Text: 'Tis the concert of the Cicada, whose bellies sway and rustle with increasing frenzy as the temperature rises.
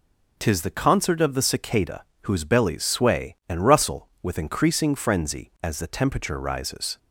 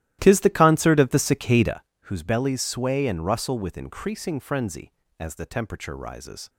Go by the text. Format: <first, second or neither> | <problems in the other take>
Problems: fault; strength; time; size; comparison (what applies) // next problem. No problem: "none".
first | starts louder than the rest; strong; until 1.9 s; 14.5 dB